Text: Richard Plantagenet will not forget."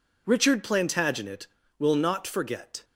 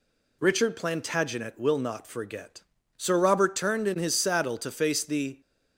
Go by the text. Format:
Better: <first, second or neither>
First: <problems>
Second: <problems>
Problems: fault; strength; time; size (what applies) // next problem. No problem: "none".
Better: first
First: none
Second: goes on to say "Sir Robert turned in his saddle to face the"; strong; from 2.9 s on; 2.4 s long